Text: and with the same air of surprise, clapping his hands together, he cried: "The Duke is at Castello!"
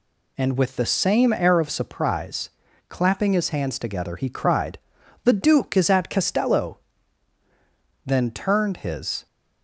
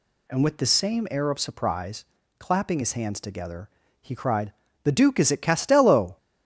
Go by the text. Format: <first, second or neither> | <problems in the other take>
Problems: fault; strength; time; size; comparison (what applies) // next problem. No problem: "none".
second | goes on to say "then turned his"; noticeable; from 8.0 s on; 1.2 s long